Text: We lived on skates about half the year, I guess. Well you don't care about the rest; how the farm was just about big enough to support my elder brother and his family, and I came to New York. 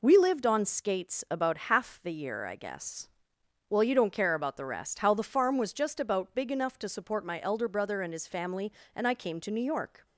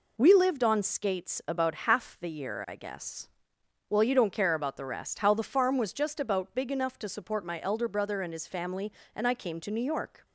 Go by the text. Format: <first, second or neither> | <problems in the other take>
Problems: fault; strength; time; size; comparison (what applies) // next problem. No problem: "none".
neither | none